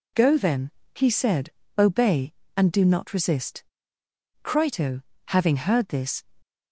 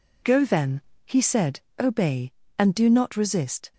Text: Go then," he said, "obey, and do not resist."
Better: second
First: goes on to say "Crito having heard this"; strong; from 4.4 s on; 1.8 s long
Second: none

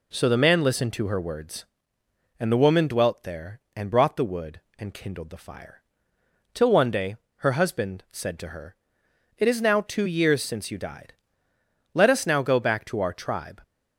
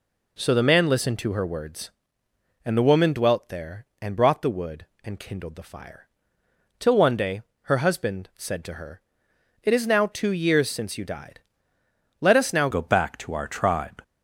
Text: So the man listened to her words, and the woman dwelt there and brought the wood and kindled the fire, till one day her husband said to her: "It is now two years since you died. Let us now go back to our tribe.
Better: first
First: pauses between "day" and "her"; slight; at 7.1 s; 0.22 s long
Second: pauses between "day" and "her"; slight; at 7.4 s; 0.22 s long // changes voice at "go"; from 12.7 s on; 1.3 s long

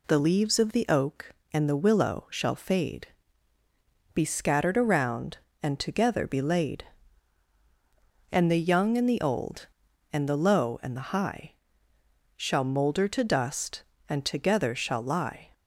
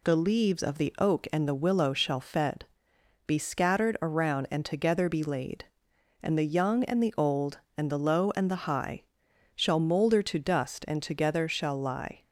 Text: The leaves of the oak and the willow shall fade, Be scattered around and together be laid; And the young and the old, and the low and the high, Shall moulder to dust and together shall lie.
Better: first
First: none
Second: says "fed" for "fade"; at 2.1 s

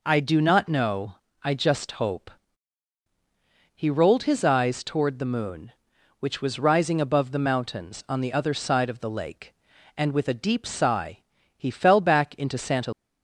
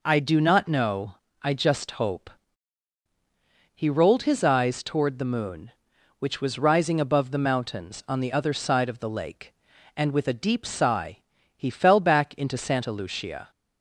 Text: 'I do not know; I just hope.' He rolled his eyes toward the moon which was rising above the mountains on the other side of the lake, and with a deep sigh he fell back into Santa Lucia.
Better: second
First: pauses between "sigh" and "he"; at 11.1 s; 0.38 s long // stops before "Lucia"; at 12.9 s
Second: pauses between "sigh" and "he"; at 11.1 s; 0.38 s long

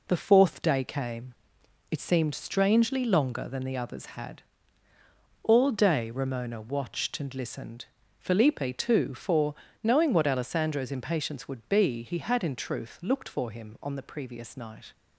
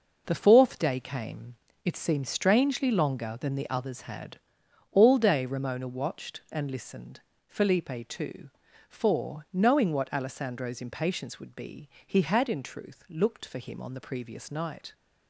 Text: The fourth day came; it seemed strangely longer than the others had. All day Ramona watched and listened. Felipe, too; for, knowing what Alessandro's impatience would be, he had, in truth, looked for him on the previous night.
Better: neither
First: none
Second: none

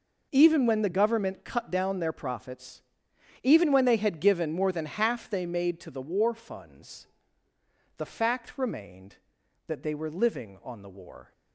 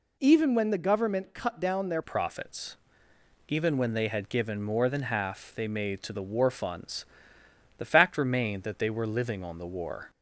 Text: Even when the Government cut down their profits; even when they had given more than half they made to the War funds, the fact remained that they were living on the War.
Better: first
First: none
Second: changes voice at "profits"; from 2.0 s on; 8.0 s long

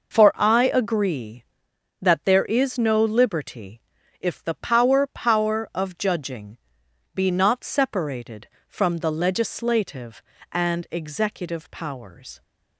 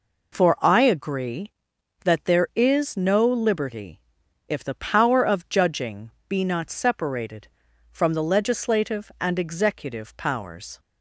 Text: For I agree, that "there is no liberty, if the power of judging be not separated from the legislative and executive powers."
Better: second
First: says "power" twice; at 5.0 s // pauses between "judging" and "be"; noticeable; at 6.5 s; 0.56 s long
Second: pauses between "judging" and "be"; slight; at 6.0 s; 0.18 s long

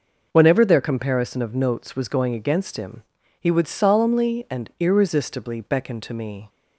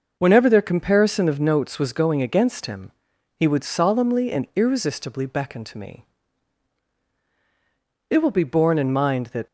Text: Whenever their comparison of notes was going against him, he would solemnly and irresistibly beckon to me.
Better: first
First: none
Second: goes on to say "It will be borne in mind that"; from 8.0 s on; 1.3 s long

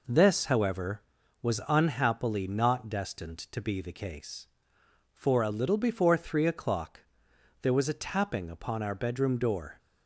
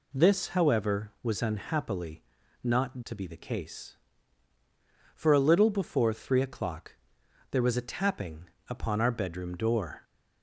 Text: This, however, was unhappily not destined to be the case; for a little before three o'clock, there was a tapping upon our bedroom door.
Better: first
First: none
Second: pauses between "unhappily" and "not"; at 2.2 s; 0.40 s long // skips "destined"; at 3.0 s // pauses between "tapping" and "upon"; slight; at 8.4 s; 0.20 s long

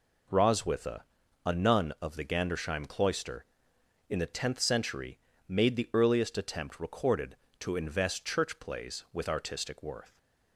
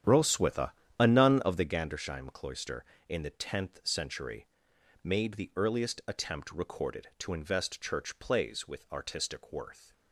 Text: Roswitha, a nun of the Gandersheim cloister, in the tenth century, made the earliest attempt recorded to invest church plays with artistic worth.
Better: first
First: none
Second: starts louder than the rest; strong; until 1.8 s; 9.5 dB

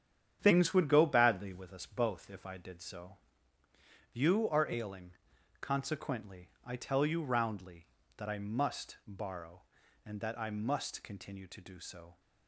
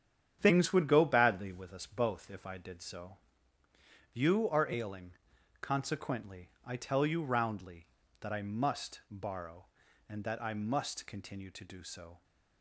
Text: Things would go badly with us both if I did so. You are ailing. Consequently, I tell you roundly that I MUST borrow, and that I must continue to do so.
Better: neither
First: starts louder than the rest; strong; until 1.4 s; 9 dB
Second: starts louder than the rest; strong; until 1.4 s; 9 dB

